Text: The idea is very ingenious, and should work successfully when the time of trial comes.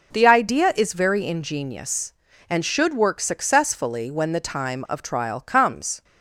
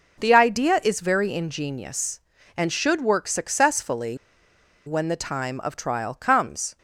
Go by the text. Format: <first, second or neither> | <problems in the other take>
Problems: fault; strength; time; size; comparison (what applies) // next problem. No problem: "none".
first | pauses between "successfully" and "when"; noticeable; at 4.1 s; 0.69 s long